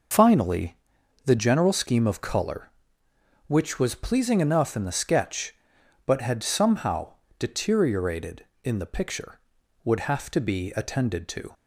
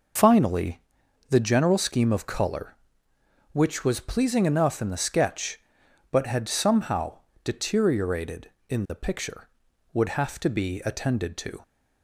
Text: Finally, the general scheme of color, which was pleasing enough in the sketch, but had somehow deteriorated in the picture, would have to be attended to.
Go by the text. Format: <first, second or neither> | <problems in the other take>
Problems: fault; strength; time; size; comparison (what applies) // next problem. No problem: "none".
neither | pauses between "somehow" and "deteriorated"; slight; the same in both